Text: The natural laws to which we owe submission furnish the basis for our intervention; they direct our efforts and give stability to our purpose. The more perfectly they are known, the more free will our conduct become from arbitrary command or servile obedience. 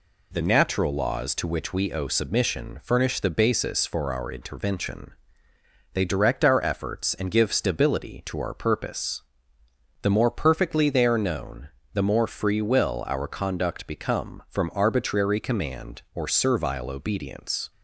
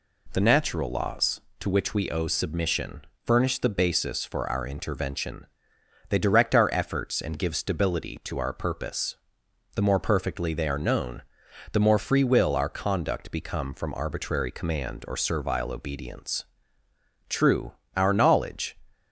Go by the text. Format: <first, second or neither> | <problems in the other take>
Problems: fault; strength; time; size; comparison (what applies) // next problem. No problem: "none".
first | pauses between "submission" and "furnish"; slight; at 3.0 s; 0.18 s long // goes on to say "True our knowledge"; from 17.2 s on; 1.4 s long